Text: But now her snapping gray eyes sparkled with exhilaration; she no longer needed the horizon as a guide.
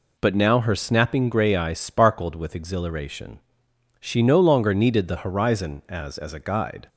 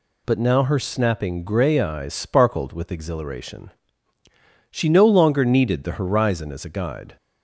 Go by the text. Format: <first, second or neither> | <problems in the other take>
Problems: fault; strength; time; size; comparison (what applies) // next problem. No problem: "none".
second | says "as" twice; at 6.1 s